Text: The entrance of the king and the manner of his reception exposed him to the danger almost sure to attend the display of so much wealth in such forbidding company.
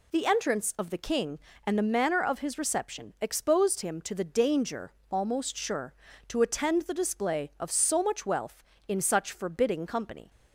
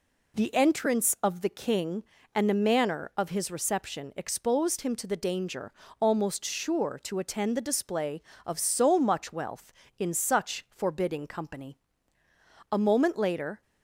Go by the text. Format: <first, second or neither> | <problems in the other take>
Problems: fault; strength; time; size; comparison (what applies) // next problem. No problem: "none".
first | pauses between "danger" and "almost"; slight; at 5.7 s; 0.30 s long; slight in the first // goes on to say "A moment later"; noticeable; from 12.7 s on; 0.90 s long